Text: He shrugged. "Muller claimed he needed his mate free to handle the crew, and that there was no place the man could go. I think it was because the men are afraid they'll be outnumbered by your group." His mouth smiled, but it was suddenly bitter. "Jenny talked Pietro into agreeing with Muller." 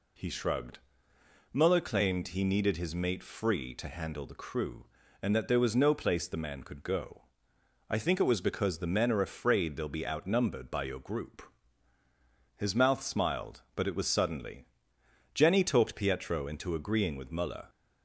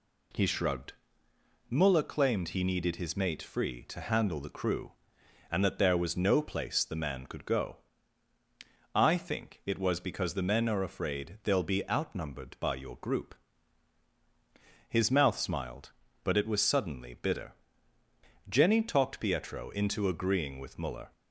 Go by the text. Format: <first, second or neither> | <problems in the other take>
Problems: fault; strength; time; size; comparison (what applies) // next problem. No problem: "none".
second | skips "bitter"; at 14.9 s